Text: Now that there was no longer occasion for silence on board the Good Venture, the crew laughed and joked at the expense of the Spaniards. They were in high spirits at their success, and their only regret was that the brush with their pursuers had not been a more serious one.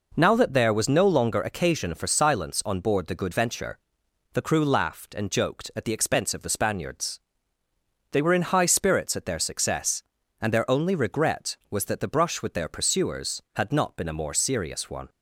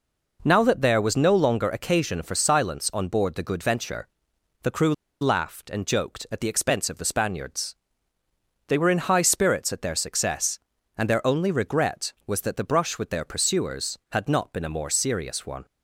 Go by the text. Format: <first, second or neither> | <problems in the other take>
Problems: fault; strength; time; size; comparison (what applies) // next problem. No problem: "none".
first | pauses between "crew" and "laughed"; slight; at 4.9 s; 0.26 s long